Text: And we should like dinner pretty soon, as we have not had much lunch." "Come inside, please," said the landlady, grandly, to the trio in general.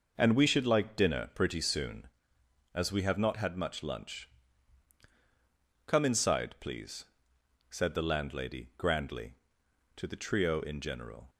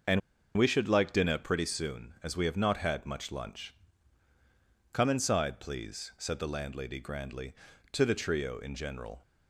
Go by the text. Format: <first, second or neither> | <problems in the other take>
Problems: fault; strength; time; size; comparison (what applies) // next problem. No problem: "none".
first | starts louder than the rest; until 1.4 s; 6 dB // pauses between "And" and "we"; at 0.2 s; 0.37 s long